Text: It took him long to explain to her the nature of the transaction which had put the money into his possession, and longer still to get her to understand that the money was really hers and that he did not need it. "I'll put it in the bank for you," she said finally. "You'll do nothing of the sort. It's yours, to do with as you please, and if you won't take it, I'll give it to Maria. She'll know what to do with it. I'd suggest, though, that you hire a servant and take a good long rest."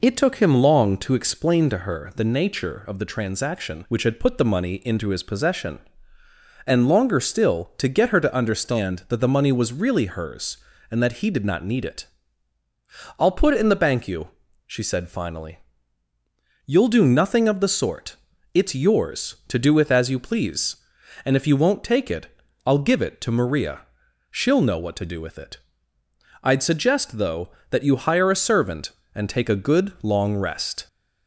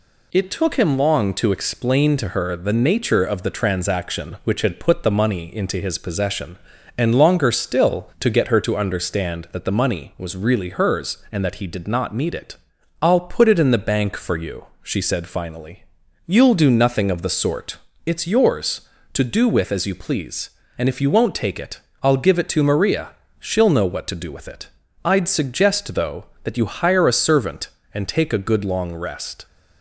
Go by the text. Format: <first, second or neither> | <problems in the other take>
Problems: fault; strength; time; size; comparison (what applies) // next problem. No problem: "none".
second | skips "for"; at 14.0 s